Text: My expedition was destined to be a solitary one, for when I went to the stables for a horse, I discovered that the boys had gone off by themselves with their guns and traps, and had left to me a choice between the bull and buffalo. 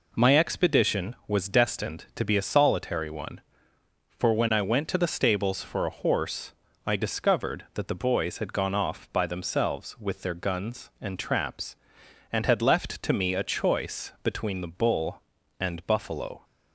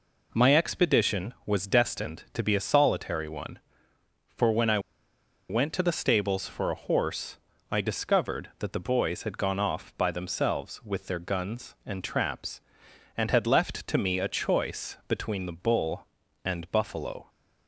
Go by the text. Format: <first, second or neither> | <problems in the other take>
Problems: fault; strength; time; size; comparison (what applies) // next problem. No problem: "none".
first | pauses between "I" and "went"; noticeable; at 4.7 s; 0.70 s long